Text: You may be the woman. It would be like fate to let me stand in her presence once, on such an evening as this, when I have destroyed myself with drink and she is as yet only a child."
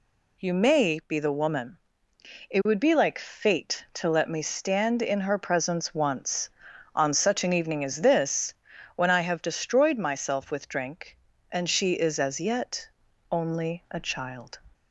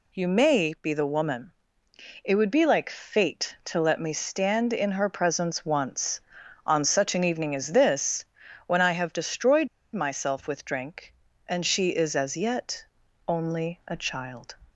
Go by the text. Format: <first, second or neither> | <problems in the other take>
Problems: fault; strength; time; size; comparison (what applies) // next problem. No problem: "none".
first | pauses between "destroyed" and "myself"; slight; at 9.6 s; 0.27 s long // pauses between "yet" and "only"; at 12.8 s; 0.42 s long; also in the first